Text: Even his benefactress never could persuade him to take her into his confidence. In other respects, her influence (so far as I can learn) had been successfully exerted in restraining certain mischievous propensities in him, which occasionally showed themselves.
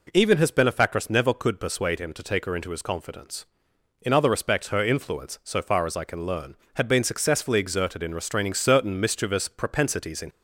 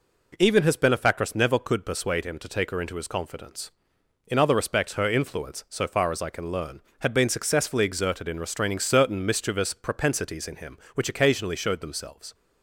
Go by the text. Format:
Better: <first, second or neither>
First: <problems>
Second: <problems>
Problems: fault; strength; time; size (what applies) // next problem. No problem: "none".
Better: second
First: stops before "him which occasionally showed themselves"; at 10.2 s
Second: none